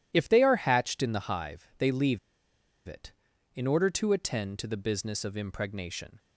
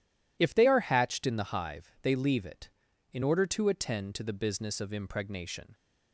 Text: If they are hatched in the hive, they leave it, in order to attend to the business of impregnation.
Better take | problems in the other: second | pauses between "leave" and "it"; noticeable; at 2.1 s; 0.69 s long

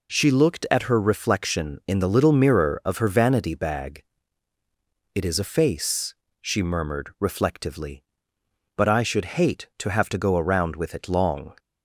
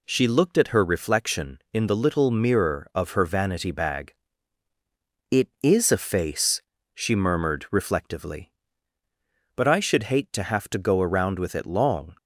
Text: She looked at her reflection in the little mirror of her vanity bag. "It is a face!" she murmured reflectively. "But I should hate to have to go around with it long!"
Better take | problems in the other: neither | none

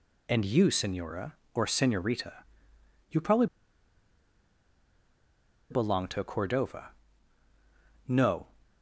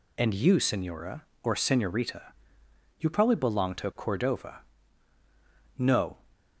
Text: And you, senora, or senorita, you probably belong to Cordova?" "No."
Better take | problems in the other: second | pauses between "probably" and "belong"; strong; at 3.4 s; 2.2 s long

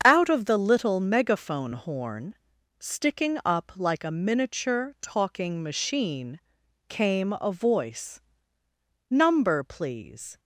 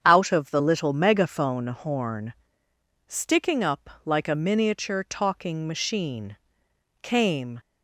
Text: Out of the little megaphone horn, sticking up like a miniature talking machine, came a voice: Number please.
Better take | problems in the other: first | starts louder than the rest; strong; until 1.0 s; 8 dB; strong in the first // pauses between "up" and "like"; slight; at 3.8 s; 0.16 s long // stops before "a voice Number please"; at 7.5 s

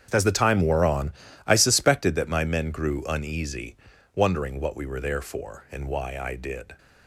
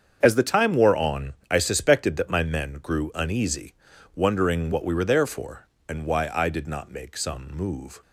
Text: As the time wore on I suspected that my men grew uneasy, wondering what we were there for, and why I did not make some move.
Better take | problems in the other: second | starts louder than the rest; strong; until 1.1 s; 8 dB; strong in the second // pauses between "on" and "I"; slight; at 1.1 s; 0.34 s long; slight in the second // stops before "not make some move"; at 6.7 s

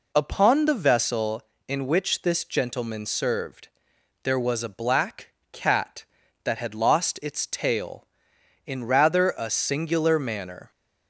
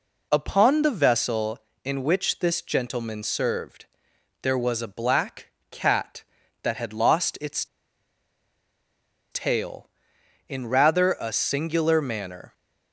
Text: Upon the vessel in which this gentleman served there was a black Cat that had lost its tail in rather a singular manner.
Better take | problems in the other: first | pauses between "served" and "there"; noticeable; at 3.8 s; 0.56 s long; noticeable in the first // pauses between "black" and "Cat"; slight; at 5.4 s; 0.20 s long; slight in the first // pauses between "its" and "tail"; strong; at 7.6 s; 1.6 s long

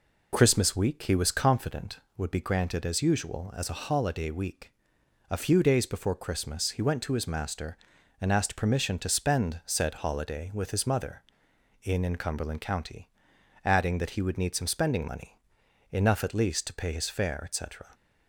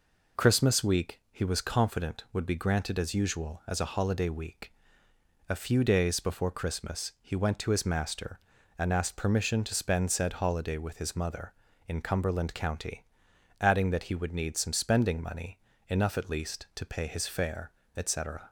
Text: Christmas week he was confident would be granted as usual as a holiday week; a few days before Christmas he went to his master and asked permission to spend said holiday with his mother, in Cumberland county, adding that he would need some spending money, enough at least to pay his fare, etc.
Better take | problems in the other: second | says "in" twice; at 12.0 s

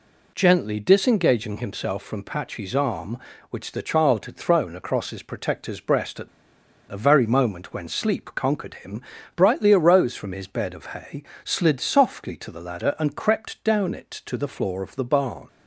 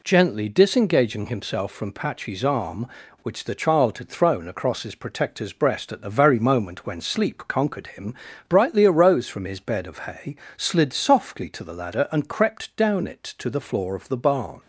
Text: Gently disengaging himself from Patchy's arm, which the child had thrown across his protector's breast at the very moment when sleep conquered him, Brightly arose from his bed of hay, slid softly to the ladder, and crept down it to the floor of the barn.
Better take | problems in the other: second | pauses between "at" and "the"; noticeable; at 6.2 s; 0.60 s long

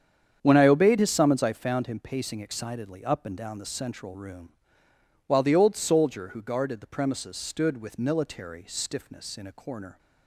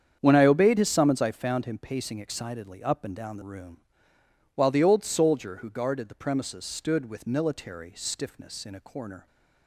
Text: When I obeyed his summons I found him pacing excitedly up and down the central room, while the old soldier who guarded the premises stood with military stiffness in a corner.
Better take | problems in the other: first | starts louder than the rest; strong; until 1.2 s; 8 dB; strong in the first // skips "central"; at 3.4 s

